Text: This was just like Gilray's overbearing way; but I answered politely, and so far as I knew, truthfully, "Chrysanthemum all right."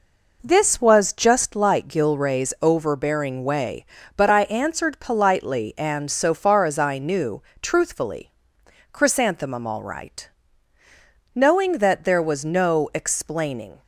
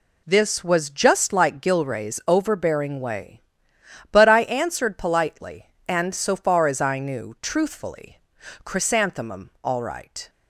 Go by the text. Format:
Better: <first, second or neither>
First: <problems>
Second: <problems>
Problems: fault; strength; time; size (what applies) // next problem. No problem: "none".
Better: second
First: goes on to say "Knowing that there was no explaining"; strong; from 11.3 s on; 2.4 s long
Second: none